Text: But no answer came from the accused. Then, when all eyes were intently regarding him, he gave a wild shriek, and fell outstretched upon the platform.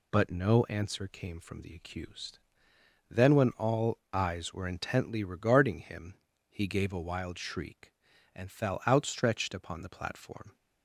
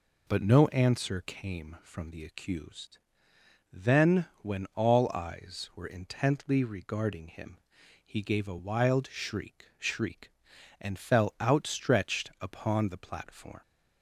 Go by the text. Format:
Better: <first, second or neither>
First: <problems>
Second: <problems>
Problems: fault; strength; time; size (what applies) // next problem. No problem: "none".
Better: first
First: none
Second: says "shriek" twice; at 9.7 s